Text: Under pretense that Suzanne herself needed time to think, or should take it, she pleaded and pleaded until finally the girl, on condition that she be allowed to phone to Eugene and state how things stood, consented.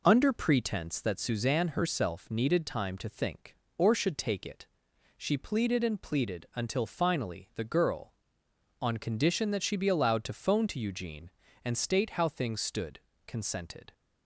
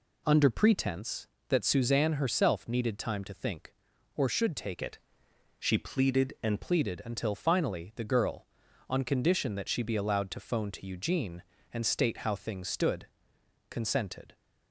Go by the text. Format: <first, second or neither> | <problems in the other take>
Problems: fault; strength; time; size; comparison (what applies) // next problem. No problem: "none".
first | changes voice from "it" to "and"; from 4.8 to 6.6 s; 1.8 s long